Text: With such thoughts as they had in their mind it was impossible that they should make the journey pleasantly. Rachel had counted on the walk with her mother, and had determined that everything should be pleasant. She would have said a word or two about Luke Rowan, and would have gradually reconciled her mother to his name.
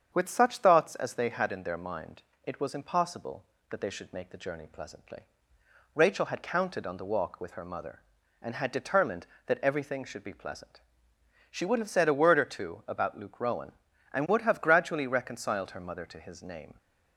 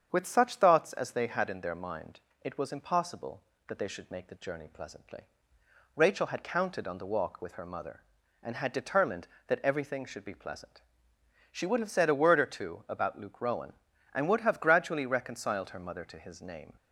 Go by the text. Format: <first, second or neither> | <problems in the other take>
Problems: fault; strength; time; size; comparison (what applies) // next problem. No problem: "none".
neither | starts louder than the rest; strong; the same in both // pauses between "mind" and "it"; slight; the same in both